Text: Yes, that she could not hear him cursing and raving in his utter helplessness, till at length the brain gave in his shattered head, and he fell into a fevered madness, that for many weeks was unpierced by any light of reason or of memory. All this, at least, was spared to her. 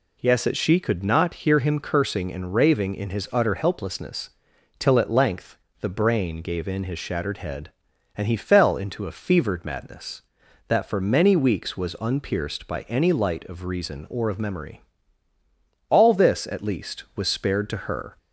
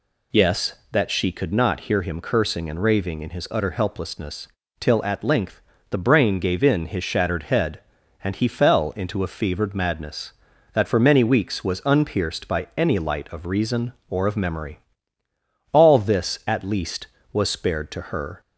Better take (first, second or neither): neither